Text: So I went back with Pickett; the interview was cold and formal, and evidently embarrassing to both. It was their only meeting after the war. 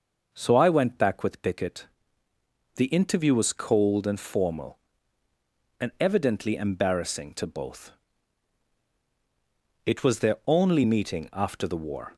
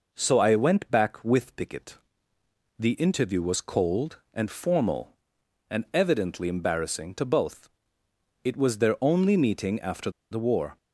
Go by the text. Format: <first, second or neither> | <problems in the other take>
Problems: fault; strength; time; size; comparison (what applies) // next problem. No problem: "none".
first | pauses between "after" and "the"; slight; at 10.0 s; 0.21 s long